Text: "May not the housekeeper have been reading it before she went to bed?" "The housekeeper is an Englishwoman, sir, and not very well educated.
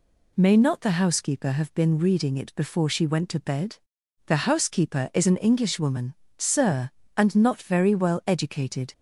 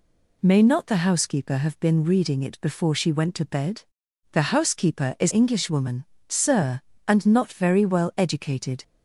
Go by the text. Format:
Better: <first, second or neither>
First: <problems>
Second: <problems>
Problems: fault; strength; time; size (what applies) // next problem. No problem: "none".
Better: first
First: none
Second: skips "an"; at 5.3 s